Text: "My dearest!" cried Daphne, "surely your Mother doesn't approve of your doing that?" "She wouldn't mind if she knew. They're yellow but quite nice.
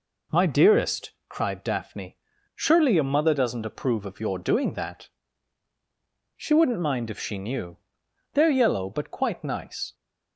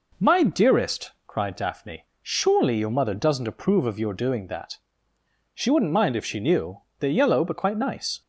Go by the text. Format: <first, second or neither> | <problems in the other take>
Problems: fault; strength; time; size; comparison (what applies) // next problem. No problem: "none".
neither | none